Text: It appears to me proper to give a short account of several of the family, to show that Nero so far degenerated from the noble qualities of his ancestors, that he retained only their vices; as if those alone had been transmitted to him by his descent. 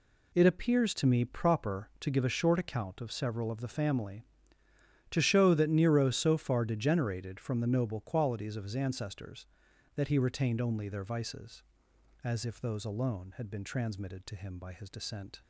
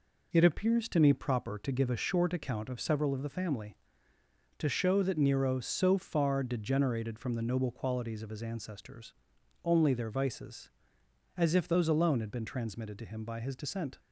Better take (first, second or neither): first